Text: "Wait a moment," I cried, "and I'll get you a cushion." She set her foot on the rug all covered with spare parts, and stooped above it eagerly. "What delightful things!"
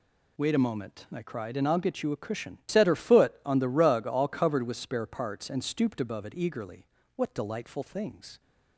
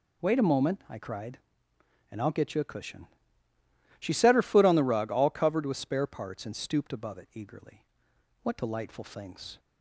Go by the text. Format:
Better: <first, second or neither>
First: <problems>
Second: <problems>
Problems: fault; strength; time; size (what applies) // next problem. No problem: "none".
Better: second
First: skips "She"; at 2.6 s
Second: none